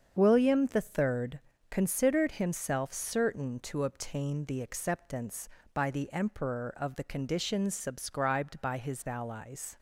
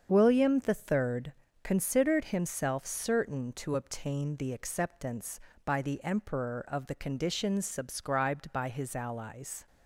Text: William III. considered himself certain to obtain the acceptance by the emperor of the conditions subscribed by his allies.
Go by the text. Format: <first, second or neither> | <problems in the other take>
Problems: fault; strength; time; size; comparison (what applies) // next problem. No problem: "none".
neither | starts louder than the rest; strong; the same in both